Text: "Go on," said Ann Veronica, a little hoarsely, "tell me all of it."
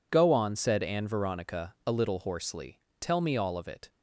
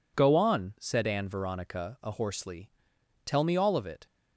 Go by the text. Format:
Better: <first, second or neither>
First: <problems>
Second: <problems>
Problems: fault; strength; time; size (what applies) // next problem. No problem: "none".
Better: first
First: none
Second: skips "little"; at 2.1 s